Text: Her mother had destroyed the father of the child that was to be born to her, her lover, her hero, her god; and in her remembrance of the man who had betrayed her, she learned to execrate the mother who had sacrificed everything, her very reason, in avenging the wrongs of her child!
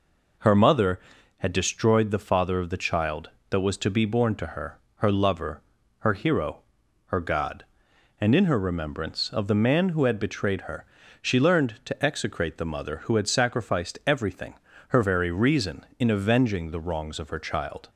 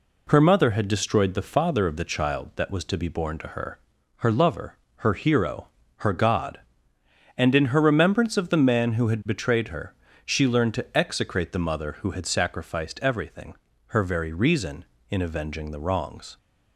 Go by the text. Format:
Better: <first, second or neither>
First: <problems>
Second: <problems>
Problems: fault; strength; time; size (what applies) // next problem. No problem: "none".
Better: first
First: none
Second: stops before "of her child"; at 16.3 s